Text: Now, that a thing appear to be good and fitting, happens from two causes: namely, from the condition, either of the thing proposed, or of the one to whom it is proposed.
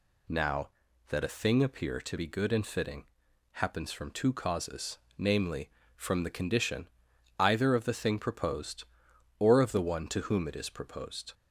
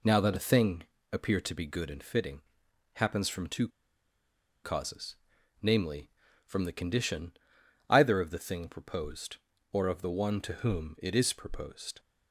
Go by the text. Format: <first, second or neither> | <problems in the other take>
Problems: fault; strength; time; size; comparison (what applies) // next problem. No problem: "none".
first | pauses between "thing" and "appear"; slight; at 0.8 s; 0.30 s long // pauses between "two" and "causes"; noticeable; at 3.6 s; 0.95 s long